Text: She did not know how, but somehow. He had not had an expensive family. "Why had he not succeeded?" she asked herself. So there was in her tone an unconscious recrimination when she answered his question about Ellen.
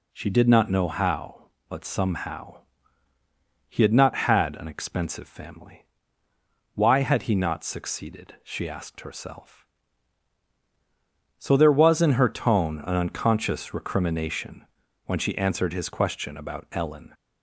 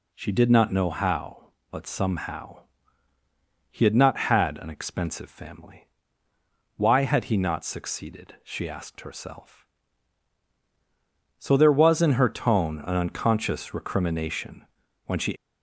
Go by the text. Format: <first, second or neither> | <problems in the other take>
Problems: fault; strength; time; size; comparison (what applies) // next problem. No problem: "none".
first | pauses between "recrimination" and "when"; at 14.6 s; 0.40 s long; also in the first // stops before "answered his question about Ellen"; at 15.3 s